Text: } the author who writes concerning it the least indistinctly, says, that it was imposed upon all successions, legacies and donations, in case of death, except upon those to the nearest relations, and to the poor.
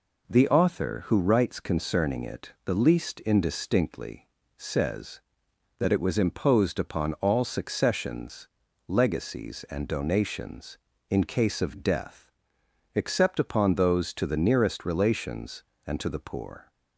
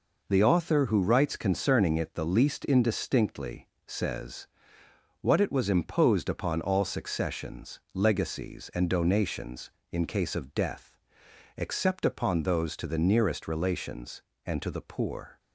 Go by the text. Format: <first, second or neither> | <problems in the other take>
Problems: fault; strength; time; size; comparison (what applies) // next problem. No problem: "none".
first | says "what" for "that"; at 5.1 s